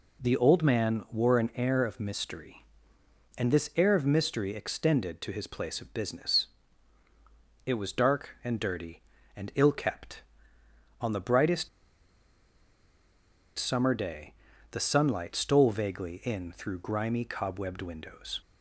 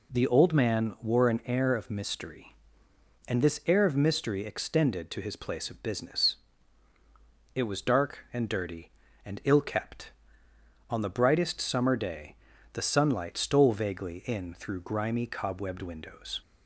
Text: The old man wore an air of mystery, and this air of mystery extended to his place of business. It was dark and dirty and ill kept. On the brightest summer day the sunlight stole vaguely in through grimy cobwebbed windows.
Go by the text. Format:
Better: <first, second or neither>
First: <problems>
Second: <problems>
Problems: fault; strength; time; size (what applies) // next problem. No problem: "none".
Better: second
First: pauses between "brightest" and "summer"; strong; at 11.6 s; 1.9 s long // pauses between "day" and "the"; at 14.3 s; 0.40 s long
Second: pauses between "day" and "the"; at 12.3 s; 0.40 s long